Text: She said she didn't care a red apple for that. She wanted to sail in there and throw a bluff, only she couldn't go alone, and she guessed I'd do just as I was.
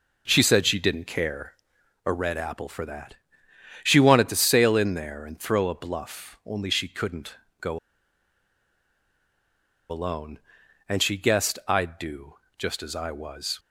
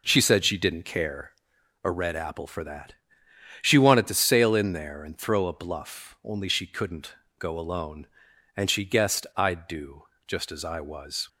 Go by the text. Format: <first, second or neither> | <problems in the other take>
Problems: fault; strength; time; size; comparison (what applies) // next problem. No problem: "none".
second | pauses between "care" and "a"; noticeable; at 1.5 s; 0.50 s long; noticeable in the second // pauses between "couldn't" and "go"; slight; at 7.3 s; 0.24 s long; slight in the second // pauses between "go" and "alone"; strong; at 7.7 s; 2.1 s long // pauses between "do" and "just"; slight; at 12.3 s; 0.24 s long; slight in the second